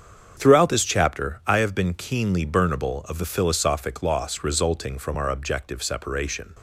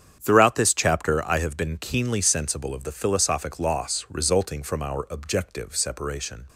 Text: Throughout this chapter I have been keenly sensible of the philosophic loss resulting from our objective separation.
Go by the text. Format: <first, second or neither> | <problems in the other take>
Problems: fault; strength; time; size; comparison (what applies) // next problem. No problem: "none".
second | starts louder than the rest; strong; until 1.3 s; 7.5 dB; strong in the second // says "burnable" for "sensible"; at 2.4 s